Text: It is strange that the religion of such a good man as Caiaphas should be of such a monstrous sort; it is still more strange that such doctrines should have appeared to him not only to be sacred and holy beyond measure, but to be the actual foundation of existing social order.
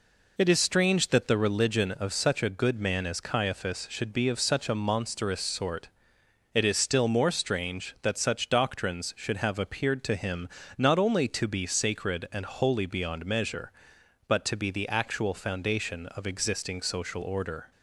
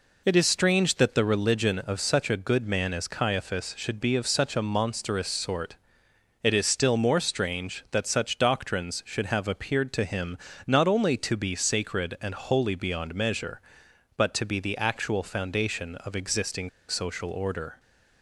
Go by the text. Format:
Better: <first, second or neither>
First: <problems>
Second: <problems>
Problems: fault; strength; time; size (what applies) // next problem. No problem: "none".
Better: first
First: pauses between "him" and "not"; slight; at 10.4 s; 0.28 s long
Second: pauses between "him" and "not"; slight; at 10.3 s; 0.28 s long // pauses between "existing" and "social"; slight; at 16.6 s; 0.18 s long